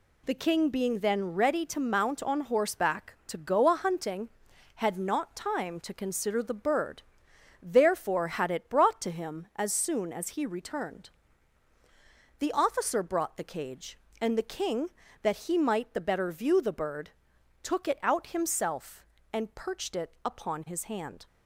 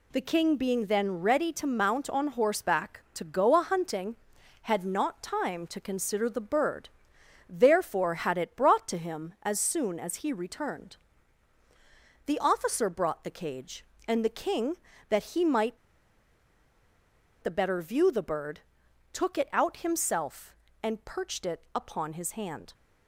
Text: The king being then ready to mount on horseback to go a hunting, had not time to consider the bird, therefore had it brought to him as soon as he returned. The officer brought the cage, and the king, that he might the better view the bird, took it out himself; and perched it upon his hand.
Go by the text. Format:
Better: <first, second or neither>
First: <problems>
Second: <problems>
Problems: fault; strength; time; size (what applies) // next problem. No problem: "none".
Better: first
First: none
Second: pauses between "might" and "the"; strong; at 15.7 s; 1.6 s long